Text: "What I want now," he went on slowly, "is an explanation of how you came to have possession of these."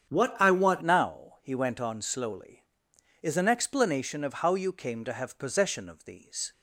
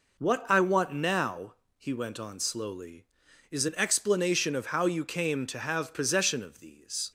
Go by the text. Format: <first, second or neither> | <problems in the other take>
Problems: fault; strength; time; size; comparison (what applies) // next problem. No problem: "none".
second | starts louder than the rest; strong; until 1.1 s; 8 dB // changes voice at "now"; from 0.8 s on; 5.7 s long